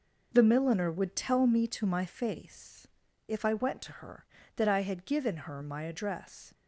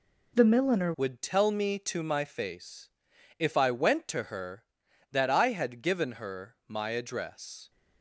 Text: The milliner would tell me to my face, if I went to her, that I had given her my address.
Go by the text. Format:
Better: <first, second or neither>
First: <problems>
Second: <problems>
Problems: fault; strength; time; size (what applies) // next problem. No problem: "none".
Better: first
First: none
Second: changes voice at "would"; from 0.9 s on; 6.7 s long